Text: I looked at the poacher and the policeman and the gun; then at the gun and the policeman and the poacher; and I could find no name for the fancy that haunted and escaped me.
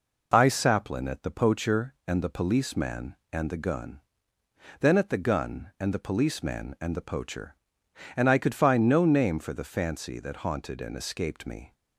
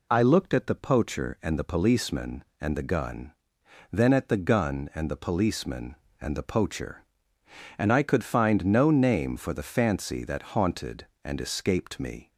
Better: second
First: says "saplin" for "looked"; at 0.4 s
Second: none

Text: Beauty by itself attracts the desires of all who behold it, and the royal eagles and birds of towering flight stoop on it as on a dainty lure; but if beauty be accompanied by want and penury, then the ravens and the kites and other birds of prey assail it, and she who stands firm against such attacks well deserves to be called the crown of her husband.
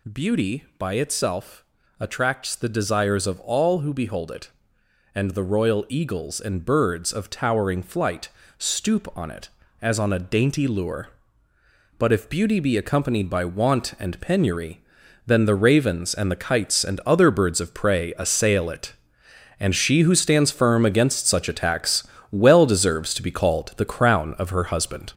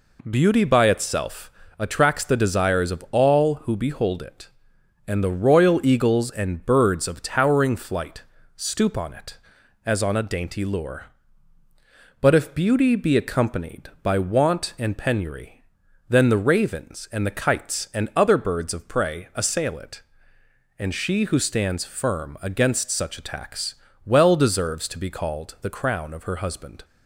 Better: second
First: gets louder; noticeable; throughout; 6 dB // pauses between "itself" and "attracts"; slight; at 1.6 s; 0.36 s long // pauses between "flight" and "stoop"; slight; at 8.2 s; 0.30 s long // pauses between "attacks" and "well"; slight; at 22.0 s; 0.28 s long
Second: pauses between "itself" and "attracts"; slight; at 1.5 s; 0.28 s long // pauses between "flight" and "stoop"; slight; at 8.2 s; 0.32 s long // pauses between "attacks" and "well"; slight; at 23.7 s; 0.30 s long

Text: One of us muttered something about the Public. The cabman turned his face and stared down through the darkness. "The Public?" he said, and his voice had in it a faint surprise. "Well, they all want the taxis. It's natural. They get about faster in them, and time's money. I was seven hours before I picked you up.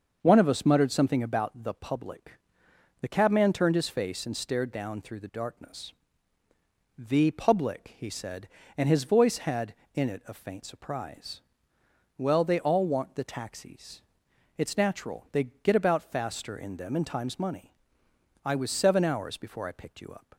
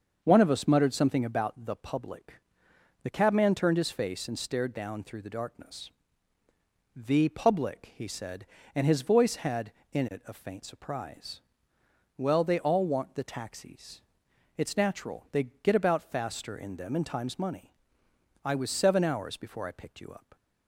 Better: neither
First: starts louder than the rest; until 1.2 s; 6.5 dB // pauses between "They" and "get"; slight; at 15.4 s; 0.18 s long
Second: starts louder than the rest; until 1.2 s; 6.5 dB // pauses between "They" and "get"; slight; at 15.4 s; 0.18 s long

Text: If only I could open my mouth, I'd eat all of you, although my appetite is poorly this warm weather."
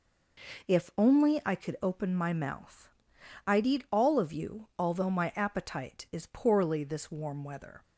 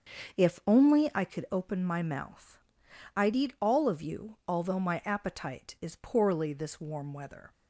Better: first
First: none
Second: starts louder than the rest; until 1.3 s; 6.5 dB

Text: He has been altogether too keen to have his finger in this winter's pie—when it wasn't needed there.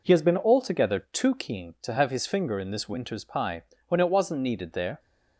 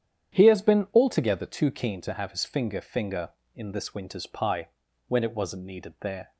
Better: first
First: none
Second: starts louder than the rest; strong; until 1.4 s; 9 dB // says "finger" twice; at 2.8 s

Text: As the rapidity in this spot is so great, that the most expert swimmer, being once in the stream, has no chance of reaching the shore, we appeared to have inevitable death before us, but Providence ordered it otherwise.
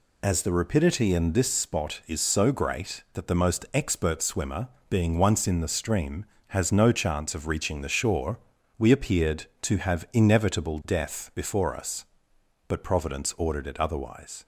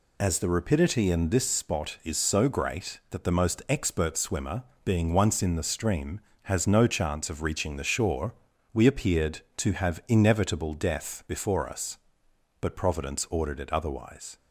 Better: neither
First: none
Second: none

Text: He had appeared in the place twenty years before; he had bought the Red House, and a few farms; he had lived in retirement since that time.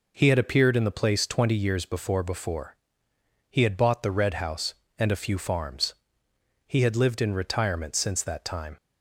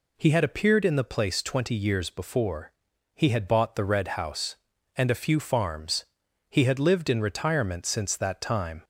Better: second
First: says "before" twice; at 2.2 s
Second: none

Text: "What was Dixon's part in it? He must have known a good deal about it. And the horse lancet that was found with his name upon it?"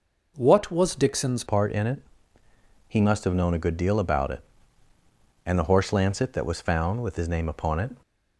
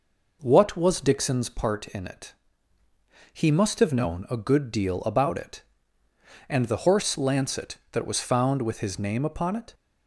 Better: second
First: changes voice at "part"; from 1.4 s on; 6.5 s long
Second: none

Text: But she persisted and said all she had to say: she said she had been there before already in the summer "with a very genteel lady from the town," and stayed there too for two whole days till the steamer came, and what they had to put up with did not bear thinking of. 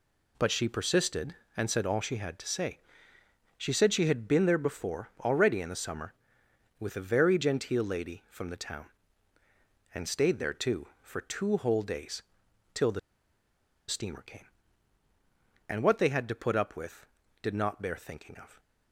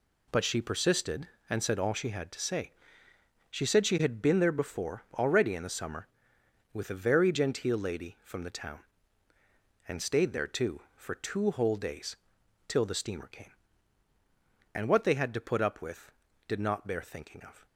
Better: second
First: pauses between "days" and "till"; noticeable; at 12.2 s; 0.52 s long // pauses between "the" and "steamer"; noticeable; at 12.9 s; 0.89 s long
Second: pauses between "days" and "till"; noticeable; at 12.1 s; 0.52 s long

